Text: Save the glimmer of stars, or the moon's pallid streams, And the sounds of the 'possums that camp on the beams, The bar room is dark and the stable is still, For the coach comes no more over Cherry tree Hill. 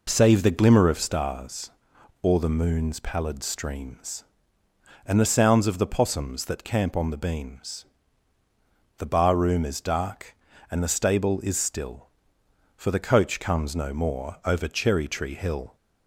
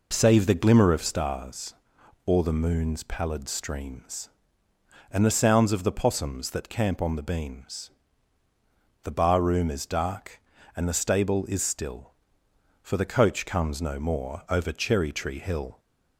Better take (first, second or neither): neither